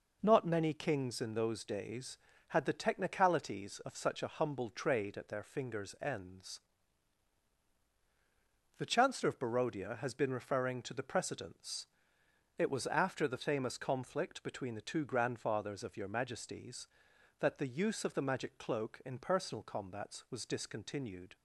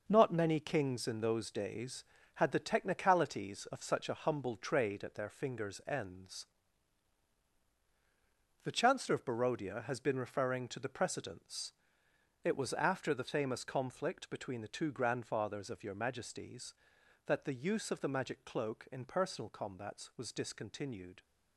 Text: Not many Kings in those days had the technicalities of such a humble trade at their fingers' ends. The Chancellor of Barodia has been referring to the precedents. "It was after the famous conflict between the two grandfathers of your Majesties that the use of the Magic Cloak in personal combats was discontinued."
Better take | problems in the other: first | gets quieter; strong; throughout; 7.5 dB

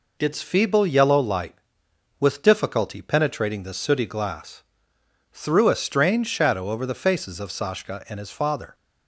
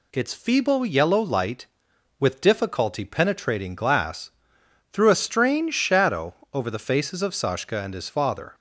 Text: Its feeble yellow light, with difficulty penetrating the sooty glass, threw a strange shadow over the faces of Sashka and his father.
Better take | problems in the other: first | skips "the sooty"; at 3.7 s // pauses between "shadow" and "over"; slight; at 6.3 s; 0.18 s long

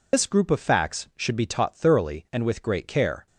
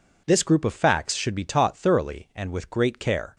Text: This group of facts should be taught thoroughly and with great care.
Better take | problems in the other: second | loses the start of "This"; at 0.1 s; 130 ms

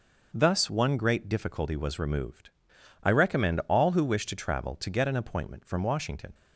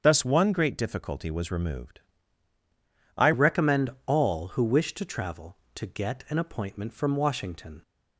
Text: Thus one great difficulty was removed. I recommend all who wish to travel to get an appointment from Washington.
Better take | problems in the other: first | starts louder than the rest; strong; until 1.0 s; 7.5 dB // changes voice at "recommend"; from 3.3 s on; 4.5 s long // pauses between "recommend" and "all"; slight; at 3.8 s; 0.16 s long

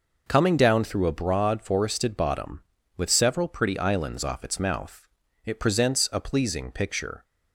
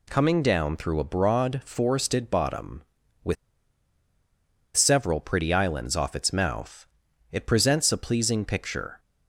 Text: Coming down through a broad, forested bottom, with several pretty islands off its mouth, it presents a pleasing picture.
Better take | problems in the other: first | pauses between "with" and "several"; strong; at 3.3 s; 1.4 s long

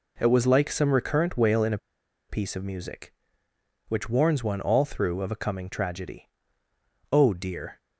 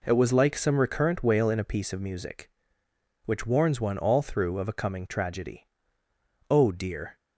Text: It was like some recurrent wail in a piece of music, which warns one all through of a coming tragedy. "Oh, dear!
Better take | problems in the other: second | pauses between "a" and "piece"; noticeable; at 1.7 s; 0.50 s long

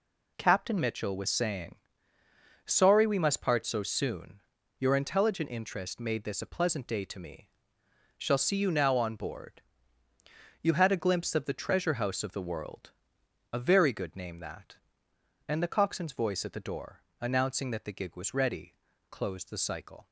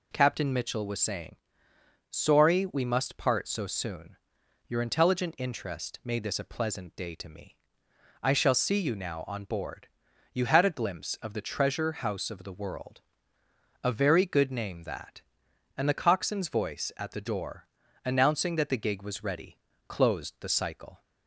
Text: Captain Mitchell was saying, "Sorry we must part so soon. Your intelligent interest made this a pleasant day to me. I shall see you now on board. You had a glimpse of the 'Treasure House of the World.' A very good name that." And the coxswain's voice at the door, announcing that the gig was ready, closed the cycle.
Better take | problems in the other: second | skips "I"; at 7.8 s

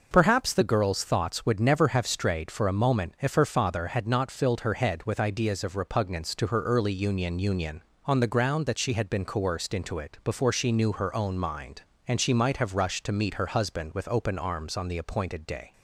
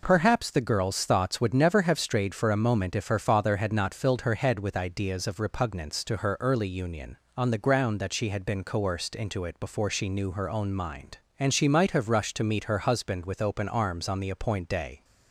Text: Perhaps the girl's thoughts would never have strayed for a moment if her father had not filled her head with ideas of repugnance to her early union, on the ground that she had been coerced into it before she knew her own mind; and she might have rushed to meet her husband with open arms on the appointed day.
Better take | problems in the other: second | says "union" twice; at 7.3 s

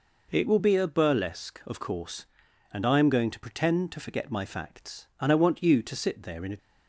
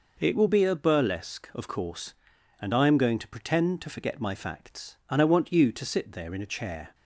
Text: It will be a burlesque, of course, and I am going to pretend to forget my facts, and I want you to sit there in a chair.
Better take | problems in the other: second | stops before "chair"; at 6.5 s

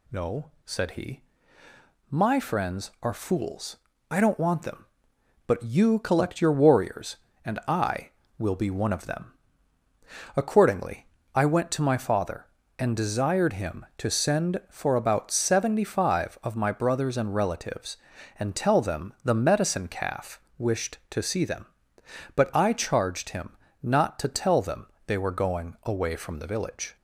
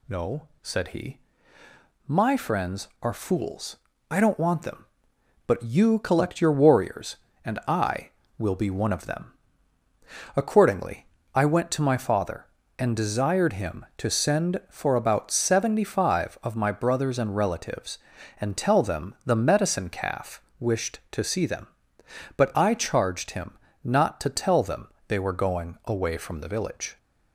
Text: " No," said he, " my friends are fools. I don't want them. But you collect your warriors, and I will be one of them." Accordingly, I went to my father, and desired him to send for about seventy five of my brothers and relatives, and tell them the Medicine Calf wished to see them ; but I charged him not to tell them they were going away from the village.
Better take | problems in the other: neither | pauses between "Calf" and "wished"; slight; the same in both // pauses between "him" and "not"; slight; the same in both // pauses between "them" and "they"; slight; the same in both

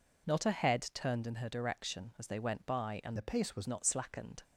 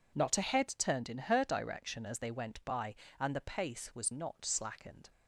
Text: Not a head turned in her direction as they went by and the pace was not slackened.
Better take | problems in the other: second | changes voice from "the" to "was"; from 3.1 to 3.6 s; 0.5 s long

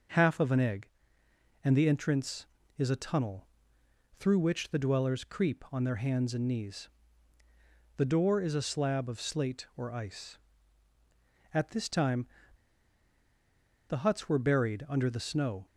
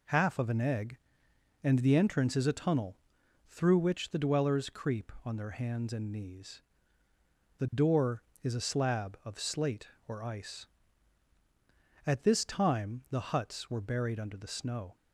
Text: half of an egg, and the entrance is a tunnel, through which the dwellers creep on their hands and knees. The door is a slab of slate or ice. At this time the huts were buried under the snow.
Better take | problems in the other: second | pauses between "time" and "the"; strong; at 12.2 s; 1.6 s long

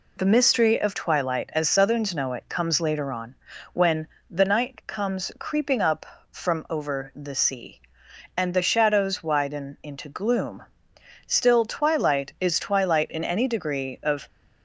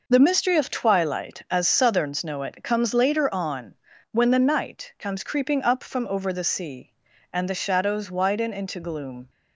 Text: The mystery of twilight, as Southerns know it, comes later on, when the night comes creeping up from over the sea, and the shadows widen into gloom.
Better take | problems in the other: second | pauses between "when" and "the"; slight; at 4.0 s; 0.24 s long // goes on to say "Still twilight is twilight in any degree of"; strong; from 11.2 s on; 3.0 s long

